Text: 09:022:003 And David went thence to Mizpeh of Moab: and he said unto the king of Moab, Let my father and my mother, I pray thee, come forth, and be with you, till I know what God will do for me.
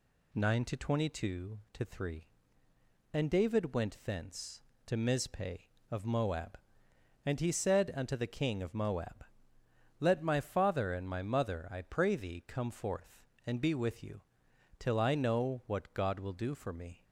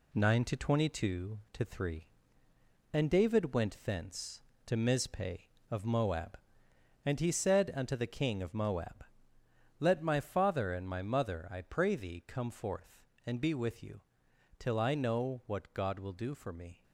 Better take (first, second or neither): first